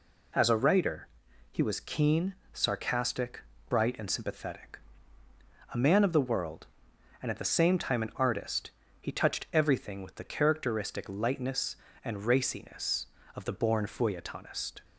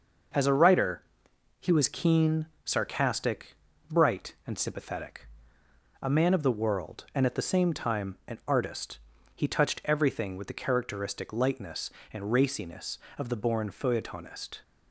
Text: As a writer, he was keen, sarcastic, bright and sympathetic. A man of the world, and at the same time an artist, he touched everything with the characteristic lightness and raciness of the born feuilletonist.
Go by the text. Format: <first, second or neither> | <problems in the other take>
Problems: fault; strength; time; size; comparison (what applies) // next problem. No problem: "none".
neither | none